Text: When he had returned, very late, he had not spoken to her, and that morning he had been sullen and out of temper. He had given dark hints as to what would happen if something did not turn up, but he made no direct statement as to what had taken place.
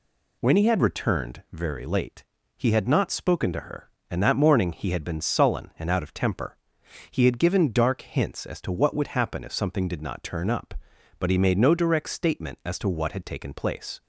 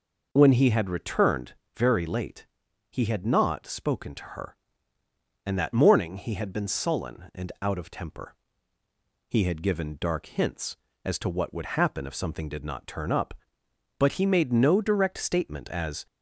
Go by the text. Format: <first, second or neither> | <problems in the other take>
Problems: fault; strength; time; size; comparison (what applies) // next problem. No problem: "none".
first | stops before "to what had taken place"; at 16.0 s